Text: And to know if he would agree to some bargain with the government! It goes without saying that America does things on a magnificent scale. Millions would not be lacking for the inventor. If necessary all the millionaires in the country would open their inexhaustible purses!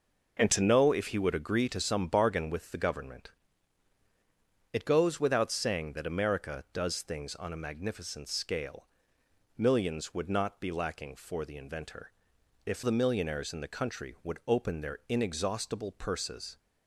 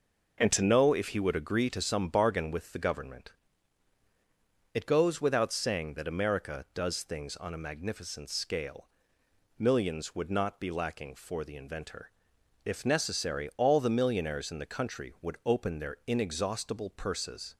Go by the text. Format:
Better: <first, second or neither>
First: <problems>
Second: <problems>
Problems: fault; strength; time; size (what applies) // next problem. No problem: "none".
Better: second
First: skips "necessary all"; at 12.8 s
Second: none